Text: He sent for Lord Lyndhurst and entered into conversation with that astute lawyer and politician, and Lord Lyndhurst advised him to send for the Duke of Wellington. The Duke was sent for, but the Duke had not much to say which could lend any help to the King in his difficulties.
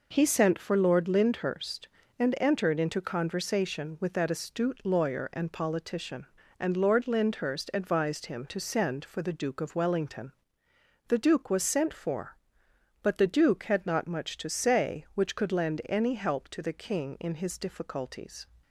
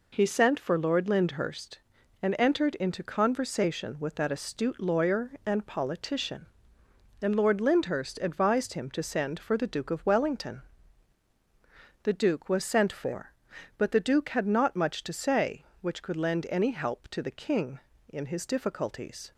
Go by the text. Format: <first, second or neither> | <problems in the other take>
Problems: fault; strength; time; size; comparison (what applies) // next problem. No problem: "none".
neither | none